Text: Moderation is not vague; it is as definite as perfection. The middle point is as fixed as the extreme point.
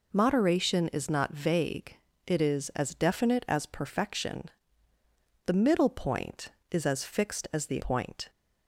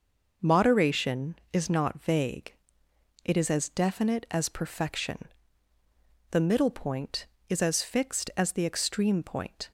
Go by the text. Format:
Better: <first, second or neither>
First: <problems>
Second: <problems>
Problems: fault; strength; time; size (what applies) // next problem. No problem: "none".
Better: second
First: skips "extreme"; at 7.7 s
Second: none